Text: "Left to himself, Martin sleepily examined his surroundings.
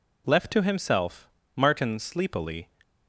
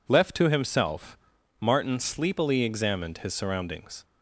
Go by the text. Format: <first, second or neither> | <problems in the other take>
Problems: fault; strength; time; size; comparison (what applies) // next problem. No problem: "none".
second | stops before "examined his surroundings"; at 2.8 s